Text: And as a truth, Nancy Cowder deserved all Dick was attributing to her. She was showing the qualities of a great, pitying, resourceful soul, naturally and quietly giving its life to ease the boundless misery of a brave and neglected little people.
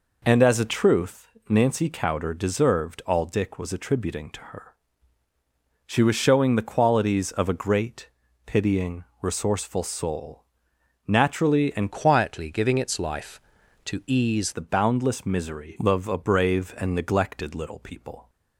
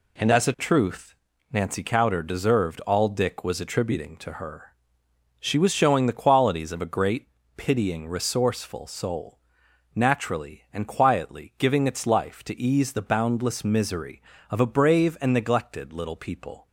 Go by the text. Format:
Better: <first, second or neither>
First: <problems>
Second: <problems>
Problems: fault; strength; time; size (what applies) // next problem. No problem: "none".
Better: second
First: changes voice from "quietly" to "ease"; from 11.9 to 14.5 s; 2.6 s long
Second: none